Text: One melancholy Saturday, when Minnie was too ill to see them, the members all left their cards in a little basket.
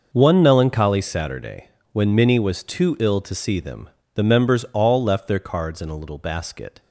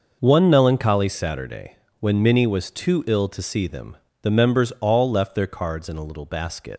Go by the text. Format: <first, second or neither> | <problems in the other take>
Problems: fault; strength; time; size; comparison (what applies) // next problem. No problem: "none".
first | leaves "basket" unfinished; at 6.7 s; 95 ms